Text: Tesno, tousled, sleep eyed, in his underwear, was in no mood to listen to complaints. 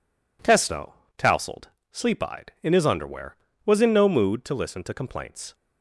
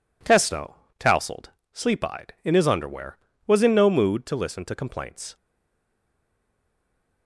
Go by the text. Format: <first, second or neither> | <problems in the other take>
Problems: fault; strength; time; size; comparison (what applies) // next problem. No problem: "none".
first | stays silent after the last word; noticeable; from 5.3 s on; 1.9 s long